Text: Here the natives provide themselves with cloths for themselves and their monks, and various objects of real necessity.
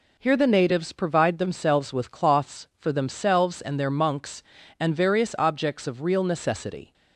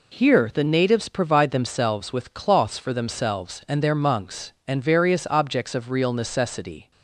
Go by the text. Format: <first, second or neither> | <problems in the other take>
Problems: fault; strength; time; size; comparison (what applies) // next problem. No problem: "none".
neither | none